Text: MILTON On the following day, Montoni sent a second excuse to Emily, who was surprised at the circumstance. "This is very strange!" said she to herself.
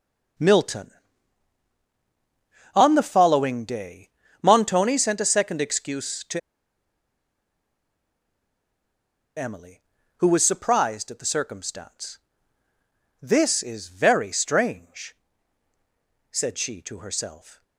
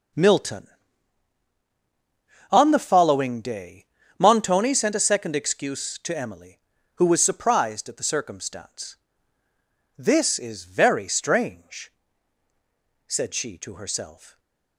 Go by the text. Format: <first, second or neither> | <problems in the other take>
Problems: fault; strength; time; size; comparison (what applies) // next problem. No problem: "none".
second | starts louder than the rest; noticeable; until 3.2 s; 6 dB // pauses between "to" and "Emily"; strong; at 6.3 s; 2.9 s long